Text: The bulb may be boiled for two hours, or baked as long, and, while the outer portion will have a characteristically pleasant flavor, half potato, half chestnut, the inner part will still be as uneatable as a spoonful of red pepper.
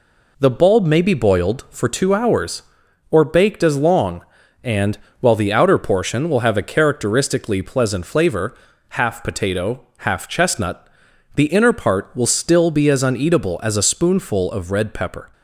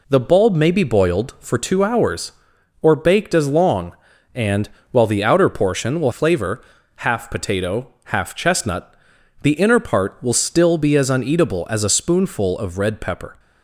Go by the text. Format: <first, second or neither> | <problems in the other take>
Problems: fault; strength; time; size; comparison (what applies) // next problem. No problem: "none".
first | skips "have a characteristically pleasant"; at 6.1 s